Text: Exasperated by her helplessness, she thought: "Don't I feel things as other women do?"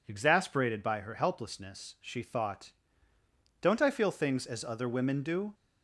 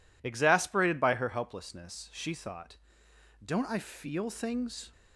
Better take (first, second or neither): first